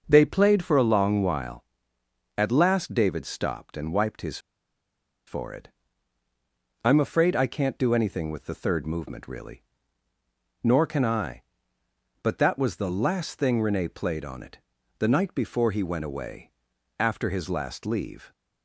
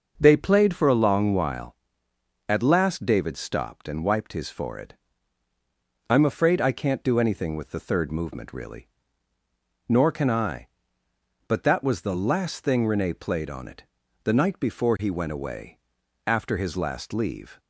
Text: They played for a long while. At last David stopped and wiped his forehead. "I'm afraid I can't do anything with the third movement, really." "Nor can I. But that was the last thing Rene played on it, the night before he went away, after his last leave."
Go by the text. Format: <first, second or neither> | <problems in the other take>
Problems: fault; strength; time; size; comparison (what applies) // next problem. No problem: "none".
second | pauses between "his" and "forehead"; noticeable; at 4.3 s; 0.89 s long